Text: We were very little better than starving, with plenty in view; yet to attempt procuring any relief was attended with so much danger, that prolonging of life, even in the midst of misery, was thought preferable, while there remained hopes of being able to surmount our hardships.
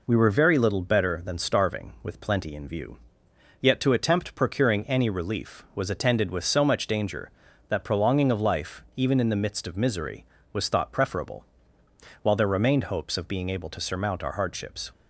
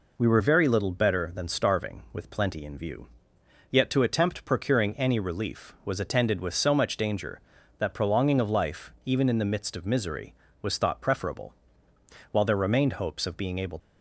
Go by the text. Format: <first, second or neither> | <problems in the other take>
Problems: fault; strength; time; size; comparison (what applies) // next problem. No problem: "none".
first | stops before "to surmount our hardships"; at 13.7 s